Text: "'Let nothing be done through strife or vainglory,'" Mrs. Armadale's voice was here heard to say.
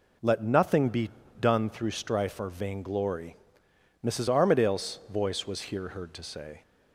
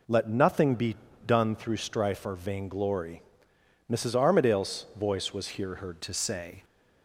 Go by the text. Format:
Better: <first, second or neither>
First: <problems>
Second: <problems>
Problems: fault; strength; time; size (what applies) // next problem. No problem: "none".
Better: first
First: pauses between "be" and "done"; slight; at 1.1 s; 0.28 s long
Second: pauses between "be" and "done"; slight; at 0.9 s; 0.28 s long // changes voice at "to"; from 6.0 s on; 0.6 s long